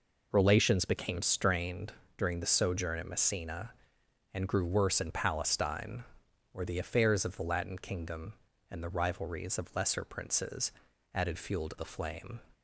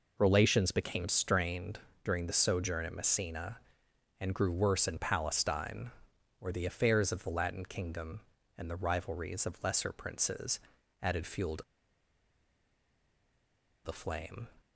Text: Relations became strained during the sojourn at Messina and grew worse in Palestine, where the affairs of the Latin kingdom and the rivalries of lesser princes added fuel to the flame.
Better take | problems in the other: first | pauses between "strained" and "during"; slight; at 1.7 s; 0.26 s long; slight in the first // pauses between "princes" and "added"; at 10.5 s; 0.44 s long; also in the first // pauses between "to" and "the"; strong; at 11.6 s; 2.2 s long

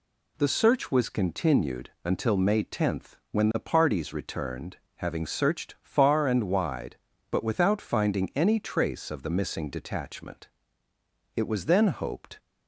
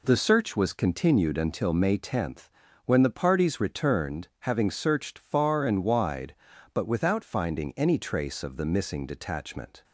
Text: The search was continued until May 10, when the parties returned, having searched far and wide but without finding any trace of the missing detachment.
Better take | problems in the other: second | goes on to say "It was then hoped"; noticeable; from 11.3 s on; 1.0 s long

